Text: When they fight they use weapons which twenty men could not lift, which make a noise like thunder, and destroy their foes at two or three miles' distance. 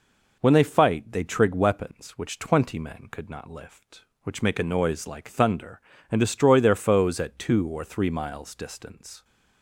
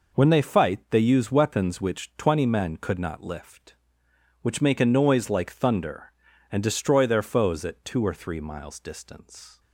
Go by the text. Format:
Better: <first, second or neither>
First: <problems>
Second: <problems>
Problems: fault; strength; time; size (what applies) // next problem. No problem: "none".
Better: second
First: says "trig" for "use"; at 1.2 s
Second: none